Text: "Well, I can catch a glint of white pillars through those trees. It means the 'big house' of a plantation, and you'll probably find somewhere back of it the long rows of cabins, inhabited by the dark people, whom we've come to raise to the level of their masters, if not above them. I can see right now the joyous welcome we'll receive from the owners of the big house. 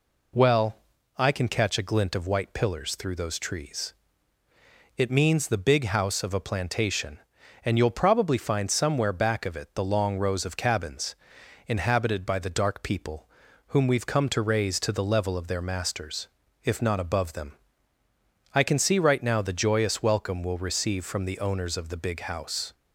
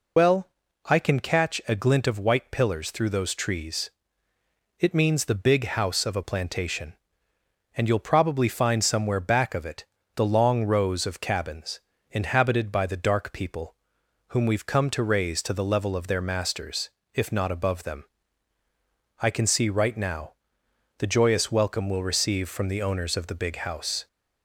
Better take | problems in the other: first | loses the start of "Well"; at 0.1 s; 75 ms // pauses between "it" and "the"; slight; at 9.8 s; 0.32 s long // pauses between "now" and "the"; noticeable; at 20.3 s; 0.64 s long

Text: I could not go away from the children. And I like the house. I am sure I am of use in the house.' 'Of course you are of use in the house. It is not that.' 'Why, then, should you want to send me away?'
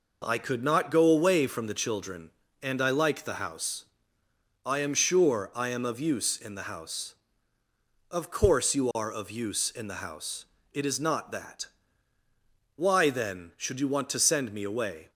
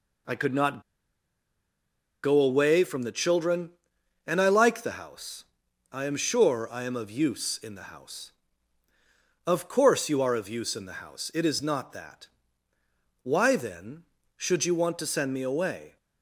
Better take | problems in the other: first | pauses between "not" and "go"; strong; at 0.8 s; 1.4 s long

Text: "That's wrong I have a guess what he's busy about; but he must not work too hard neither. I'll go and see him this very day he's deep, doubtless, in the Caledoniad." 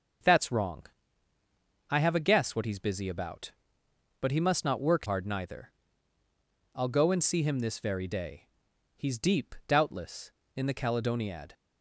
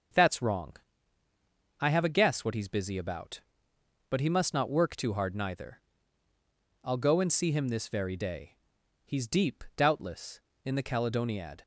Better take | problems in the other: second | starts louder than the rest; noticeable; until 2.2 s; 6 dB; also in the second // pauses between "wrong" and "I"; at 0.8 s; 1.0 s long; also in the second // skips "too"; at 5.0 s // pauses between "day" and "he's"; noticeable; at 8.4 s; 0.48 s long; noticeable in the second

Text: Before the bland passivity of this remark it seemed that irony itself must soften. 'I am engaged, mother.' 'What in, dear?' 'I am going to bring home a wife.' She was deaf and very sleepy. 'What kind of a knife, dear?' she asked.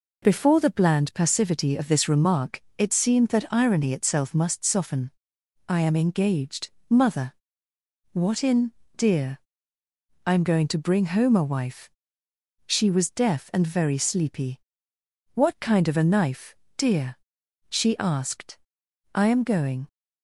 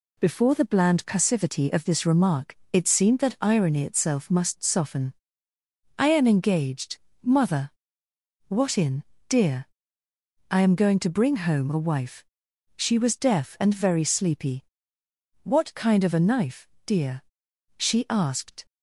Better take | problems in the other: second | pauses between "remark" and "it"; slight; at 2.6 s; 0.16 s long; slight in the second // goes on to say "I am going"; noticeable; from 19.1 s on; 0.74 s long

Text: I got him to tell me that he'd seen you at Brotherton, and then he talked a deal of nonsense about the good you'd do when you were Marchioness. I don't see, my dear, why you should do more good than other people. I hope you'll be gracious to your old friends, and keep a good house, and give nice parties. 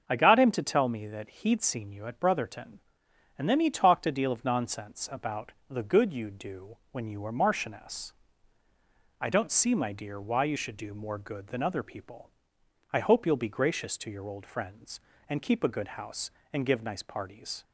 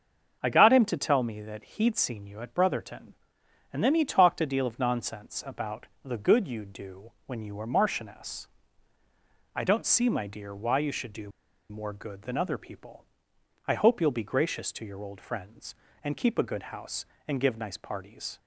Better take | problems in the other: first | starts louder than the rest; until 1.4 s; 6.5 dB; also in the first // pauses between "about" and "the"; slight; at 5.8 s; 0.18 s long; slight in the first // pauses between "do" and "more"; at 11.3 s; 0.39 s long

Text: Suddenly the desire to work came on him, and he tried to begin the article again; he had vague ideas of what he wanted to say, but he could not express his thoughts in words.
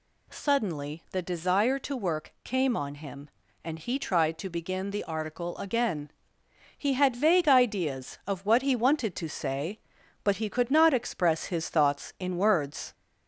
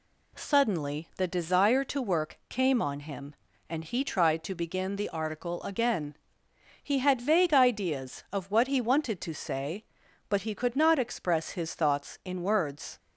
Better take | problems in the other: second | gets louder; slight; throughout; 2 dB

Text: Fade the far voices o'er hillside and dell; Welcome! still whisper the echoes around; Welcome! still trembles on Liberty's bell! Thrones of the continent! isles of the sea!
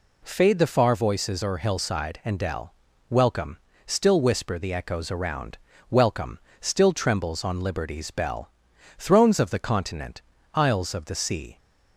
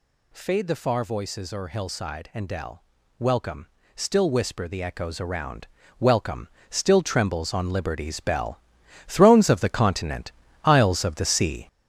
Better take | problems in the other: first | gets louder; throughout; 6.5 dB

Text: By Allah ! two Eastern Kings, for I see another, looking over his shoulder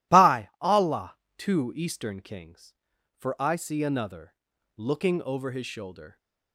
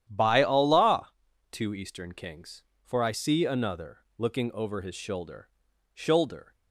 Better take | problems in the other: first | starts louder than the rest; strong; until 1.1 s; 10.5 dB // says "shoulder" twice; at 5.9 s

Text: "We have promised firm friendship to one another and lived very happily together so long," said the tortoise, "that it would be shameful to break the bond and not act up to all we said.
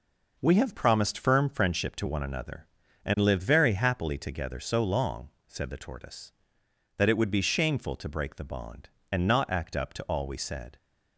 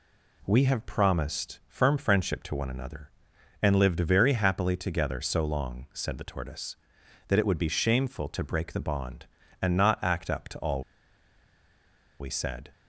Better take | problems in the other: first | pauses between "all" and "we"; strong; at 10.8 s; 1.3 s long

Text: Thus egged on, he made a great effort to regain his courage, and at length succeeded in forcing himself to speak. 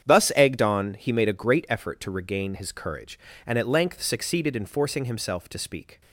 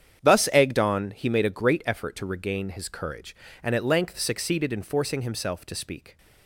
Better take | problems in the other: neither | starts louder than the rest; strong; the same in both

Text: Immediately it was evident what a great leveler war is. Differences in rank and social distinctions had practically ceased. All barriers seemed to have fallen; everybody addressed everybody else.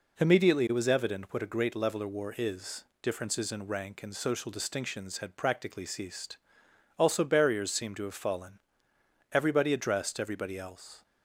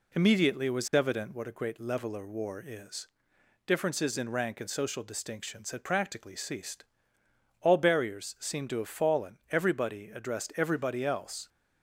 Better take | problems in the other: second | says "Also" for "All"; at 6.9 s

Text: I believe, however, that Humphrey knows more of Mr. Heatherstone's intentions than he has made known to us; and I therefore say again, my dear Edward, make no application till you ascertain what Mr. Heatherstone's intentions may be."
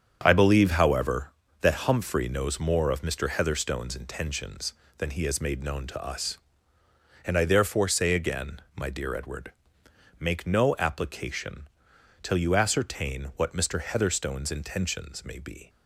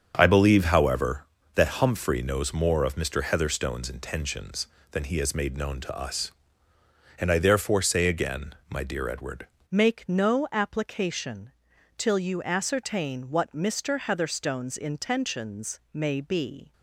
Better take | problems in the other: first | starts louder than the rest; until 1.1 s; 7 dB; strong in the first // changes voice at "make"; from 9.7 s on; 7.0 s long // pauses between "application" and "till"; noticeable; at 11.5 s; 0.46 s long; noticeable in the first

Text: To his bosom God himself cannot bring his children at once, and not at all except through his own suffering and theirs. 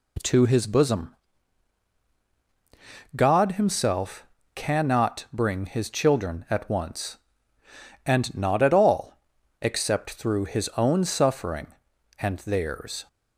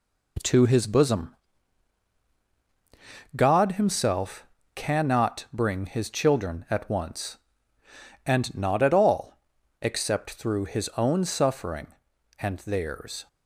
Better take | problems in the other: first | gets quieter; noticeable; throughout; 5 dB // pauses between "bosom" and "God"; strong; at 1.3 s; 2.0 s long; strong in the first // pauses between "himself" and "cannot"; slight; at 4.4 s; 0.30 s long; slight in the first // pauses between "all" and "except"; noticeable; at 9.3 s; 0.48 s long; noticeable in the first

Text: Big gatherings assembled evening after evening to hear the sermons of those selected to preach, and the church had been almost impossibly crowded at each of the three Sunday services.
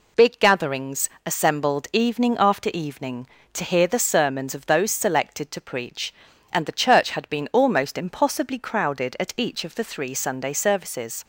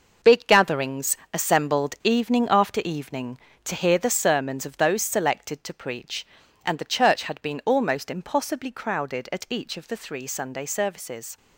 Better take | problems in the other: first | gets quieter; strong; throughout; 8.5 dB // pauses between "gatherings" and "assembled"; slight; at 1.1 s; 0.16 s long; slight in the first

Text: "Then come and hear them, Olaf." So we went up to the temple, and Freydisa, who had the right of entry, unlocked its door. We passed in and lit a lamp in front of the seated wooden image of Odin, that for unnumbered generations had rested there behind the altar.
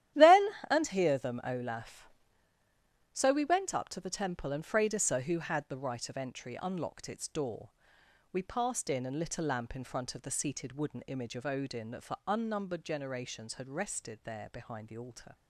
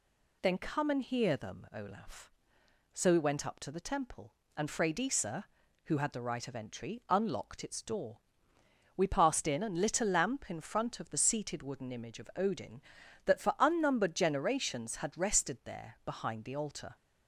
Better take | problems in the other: second | starts louder than the rest; strong; until 1.3 s; 12.5 dB // skips "come"; at 0.6 s

